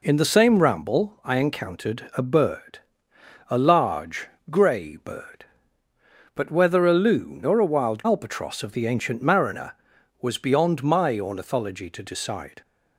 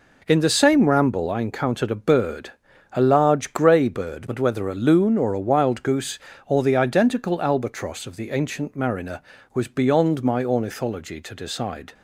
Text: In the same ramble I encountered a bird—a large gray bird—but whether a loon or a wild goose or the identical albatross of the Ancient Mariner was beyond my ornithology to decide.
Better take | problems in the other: second | pauses between "large" and "gray"; slight; at 4.2 s; 0.22 s long // skips "goose or the identical"; at 8.0 s

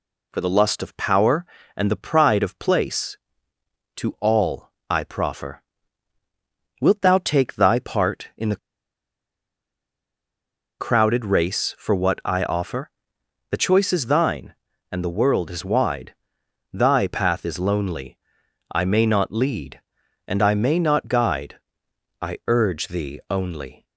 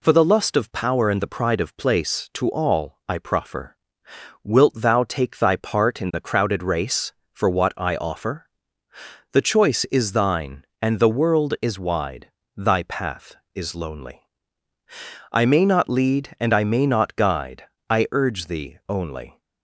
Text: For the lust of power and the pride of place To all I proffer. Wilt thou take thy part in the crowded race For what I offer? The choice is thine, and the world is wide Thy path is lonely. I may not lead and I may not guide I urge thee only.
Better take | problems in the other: second | pauses between "all" and "I"; slight; at 4.6 s; 0.20 s long // pauses between "the" and "crowded"; strong; at 8.5 s; 2.2 s long // pauses between "wide" and "Thy"; noticeable; at 16.1 s; 0.58 s long; slight in the second // pauses between "guide" and "I"; noticeable; at 21.5 s; 0.66 s long; slight in the second

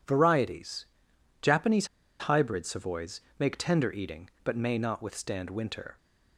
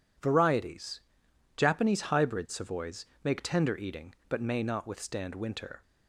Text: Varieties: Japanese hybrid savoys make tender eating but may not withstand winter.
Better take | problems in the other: second | pauses between "Japanese" and "hybrid"; slight; at 1.8 s; 0.33 s long // pauses between "savoys" and "make"; slight; at 3.2 s; 0.18 s long; slight in the second

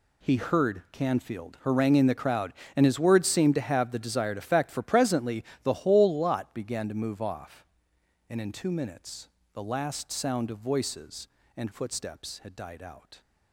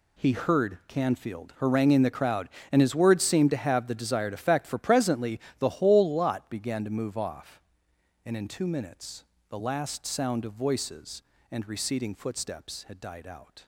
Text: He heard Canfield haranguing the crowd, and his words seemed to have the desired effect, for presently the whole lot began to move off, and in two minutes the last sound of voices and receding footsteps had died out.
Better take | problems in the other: second | pauses between "presently" and "the"; slight; at 5.4 s; 0.20 s long; slight in the second // pauses between "minutes" and "the"; slight; at 9.2 s; 0.26 s long; slight in the second // skips "receding"; at 11.7 s

